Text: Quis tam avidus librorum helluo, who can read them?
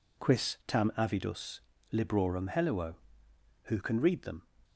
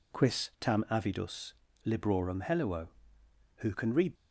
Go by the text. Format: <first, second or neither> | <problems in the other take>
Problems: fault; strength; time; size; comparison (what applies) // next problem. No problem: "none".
first | pauses between "avidus" and "librorum"; slight; at 1.5 s; 0.34 s long; slight in the first // stops before "them"; at 4.1 s